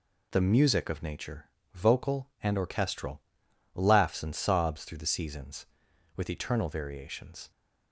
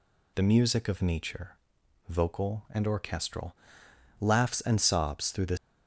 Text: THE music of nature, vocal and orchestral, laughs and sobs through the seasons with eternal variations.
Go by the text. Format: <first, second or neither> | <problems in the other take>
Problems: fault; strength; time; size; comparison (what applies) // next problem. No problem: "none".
first | stops before "seasons with eternal variations"; at 5.5 s